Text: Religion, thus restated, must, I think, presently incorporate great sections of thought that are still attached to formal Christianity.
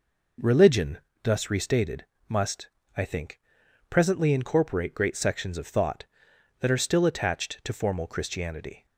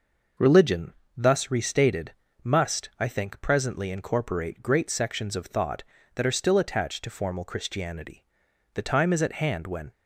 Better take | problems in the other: first | goes on to say "The time is at hand when"; noticeable; from 8.7 s on; 1.1 s long

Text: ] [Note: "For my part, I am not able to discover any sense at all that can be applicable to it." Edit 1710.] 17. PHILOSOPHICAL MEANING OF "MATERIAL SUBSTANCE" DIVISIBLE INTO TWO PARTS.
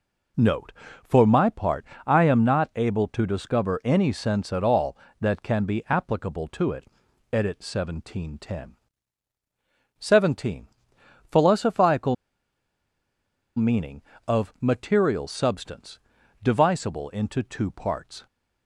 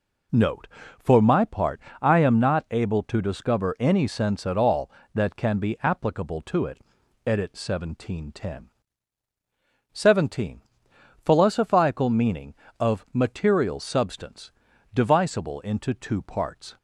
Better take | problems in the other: second | pauses between "PHILOSOPHICAL" and "MEANING"; strong; at 12.1 s; 1.4 s long // pauses between "SUBSTANCE" and "DIVISIBLE"; at 15.9 s; 0.44 s long; also in the second

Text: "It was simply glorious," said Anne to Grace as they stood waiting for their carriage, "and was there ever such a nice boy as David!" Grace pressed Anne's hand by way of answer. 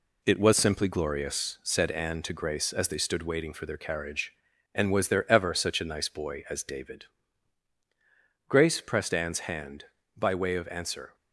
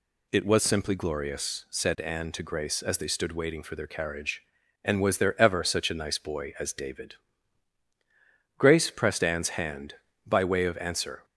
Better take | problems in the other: second | gets quieter; noticeable; throughout; 5.5 dB

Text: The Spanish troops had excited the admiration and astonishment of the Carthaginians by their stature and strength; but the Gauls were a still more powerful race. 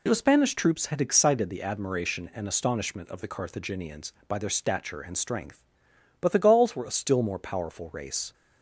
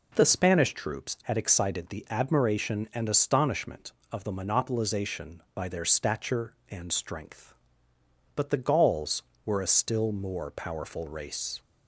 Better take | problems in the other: first | says "Monopolization" for "Carthaginians"; at 4.3 s

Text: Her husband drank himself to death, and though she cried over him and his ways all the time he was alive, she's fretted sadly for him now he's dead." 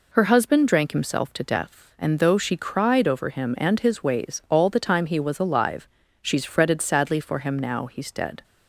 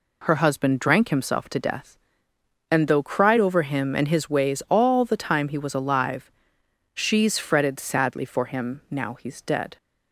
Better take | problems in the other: first | skips "she"; at 3.0 s

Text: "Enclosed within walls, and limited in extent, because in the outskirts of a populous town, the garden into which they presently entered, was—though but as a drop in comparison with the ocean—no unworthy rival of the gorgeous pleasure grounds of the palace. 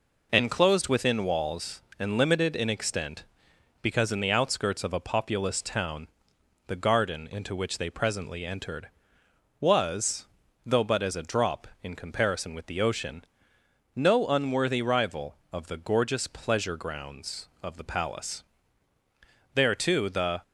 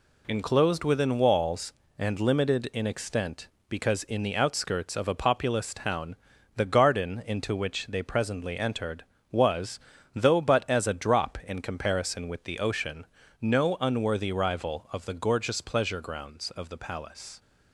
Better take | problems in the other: second | goes on to say "There too the"; noticeable; from 19.5 s on; 0.86 s long

